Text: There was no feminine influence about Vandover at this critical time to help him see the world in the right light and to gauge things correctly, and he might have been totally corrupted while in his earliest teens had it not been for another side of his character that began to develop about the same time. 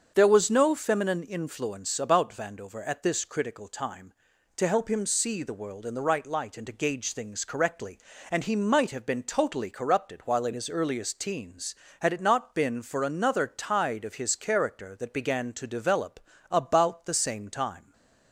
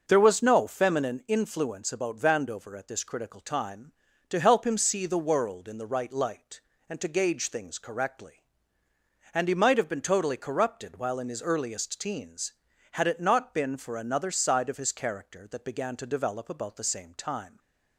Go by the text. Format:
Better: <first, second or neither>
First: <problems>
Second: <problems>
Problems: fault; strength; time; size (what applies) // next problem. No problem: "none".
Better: second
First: starts louder than the rest; until 1.1 s; 6.5 dB // says "tide" for "side"; at 13.4 s // pauses between "develop" and "about"; slight; at 16.2 s; 0.28 s long // stays silent after the last word; slight; from 17.8 s on; 0.5 s long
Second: starts louder than the rest; noticeable; until 1.0 s; 6 dB // stays silent after the last word; slight; from 17.4 s on; 0.5 s long